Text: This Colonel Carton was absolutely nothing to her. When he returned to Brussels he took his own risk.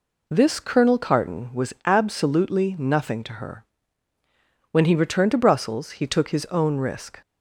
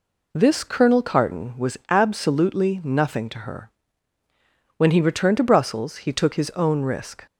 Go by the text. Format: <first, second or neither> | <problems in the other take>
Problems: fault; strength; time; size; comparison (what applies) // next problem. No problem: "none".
neither | none